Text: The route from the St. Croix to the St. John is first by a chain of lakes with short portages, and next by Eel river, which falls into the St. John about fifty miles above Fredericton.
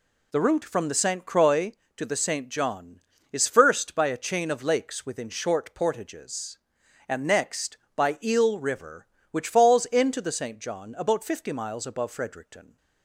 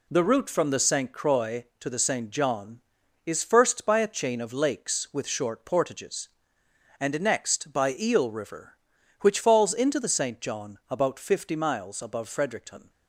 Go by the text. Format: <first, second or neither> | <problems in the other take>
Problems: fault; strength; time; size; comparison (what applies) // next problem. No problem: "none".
second | says "within" for "with"; at 5.0 s